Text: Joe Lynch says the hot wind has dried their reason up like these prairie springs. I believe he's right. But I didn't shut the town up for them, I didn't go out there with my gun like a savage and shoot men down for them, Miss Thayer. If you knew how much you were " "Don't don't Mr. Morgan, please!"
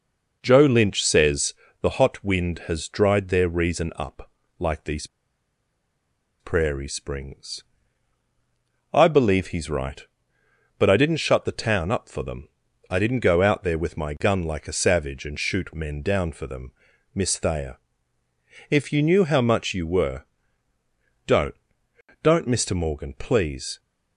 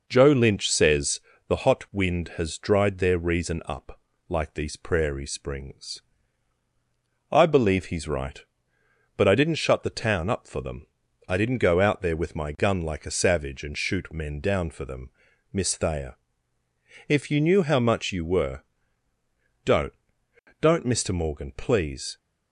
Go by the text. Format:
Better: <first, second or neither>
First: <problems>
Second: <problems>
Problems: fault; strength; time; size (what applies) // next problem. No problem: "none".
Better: second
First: pauses between "says" and "the"; slight; at 1.5 s; 0.28 s long // pauses between "up" and "like"; slight; at 4.2 s; 0.28 s long // pauses between "these" and "prairie"; strong; at 5.0 s; 1.3 s long // pauses between "Don't" and "don't"; noticeable; at 21.5 s; 0.66 s long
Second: pauses between "says" and "the"; slight; at 1.1 s; 0.28 s long // pauses between "up" and "like"; slight; at 3.9 s; 0.28 s long // pauses between "Don't" and "don't"; noticeable; at 19.9 s; 0.66 s long